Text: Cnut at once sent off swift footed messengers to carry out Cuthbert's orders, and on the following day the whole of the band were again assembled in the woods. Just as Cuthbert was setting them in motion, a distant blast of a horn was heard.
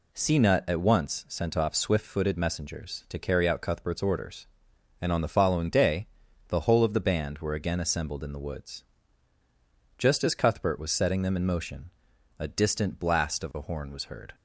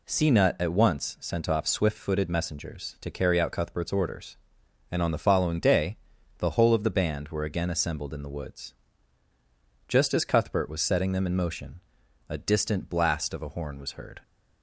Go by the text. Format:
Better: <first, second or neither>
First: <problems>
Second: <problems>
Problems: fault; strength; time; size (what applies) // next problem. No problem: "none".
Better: neither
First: pauses between "day" and "the"; at 6.0 s; 0.42 s long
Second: pauses between "day" and "the"; at 5.9 s; 0.42 s long